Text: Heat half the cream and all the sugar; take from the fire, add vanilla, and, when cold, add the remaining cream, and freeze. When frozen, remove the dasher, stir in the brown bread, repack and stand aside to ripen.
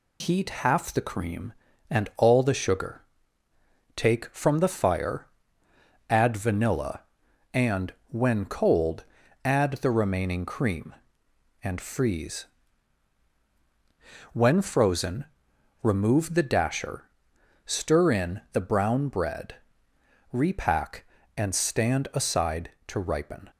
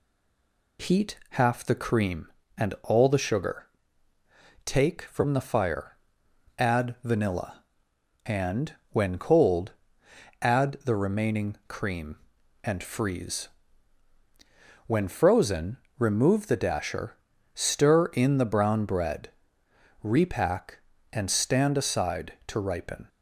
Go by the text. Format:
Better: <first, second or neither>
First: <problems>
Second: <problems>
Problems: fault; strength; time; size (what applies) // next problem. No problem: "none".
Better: first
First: none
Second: stays silent before the first word; slight; until 0.7 s; 0.7 s long